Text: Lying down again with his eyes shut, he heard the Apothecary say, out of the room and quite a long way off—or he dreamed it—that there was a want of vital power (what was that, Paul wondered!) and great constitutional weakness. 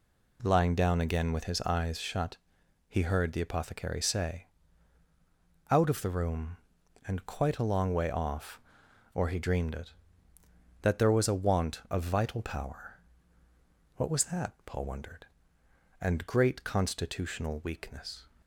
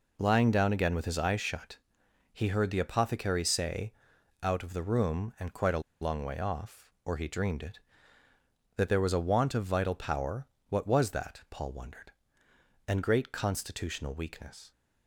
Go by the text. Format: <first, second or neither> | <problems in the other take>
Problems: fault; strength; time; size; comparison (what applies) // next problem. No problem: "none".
first | pauses between "a" and "long"; slight; at 5.8 s; 0.20 s long